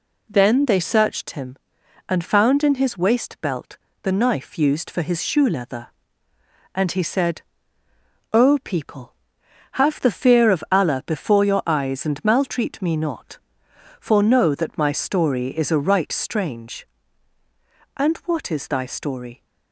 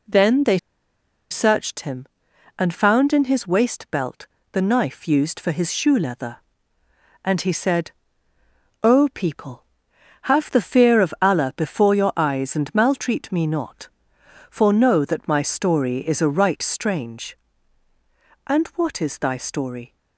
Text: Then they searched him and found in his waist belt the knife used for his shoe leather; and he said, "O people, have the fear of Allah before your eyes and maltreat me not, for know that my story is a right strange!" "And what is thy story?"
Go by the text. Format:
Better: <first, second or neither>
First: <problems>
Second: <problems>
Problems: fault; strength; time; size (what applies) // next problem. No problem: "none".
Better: first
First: pauses between "belt" and "the"; slight; at 3.7 s; 0.24 s long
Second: pauses between "they" and "searched"; noticeable; at 0.5 s; 0.72 s long // pauses between "belt" and "the"; slight; at 4.2 s; 0.24 s long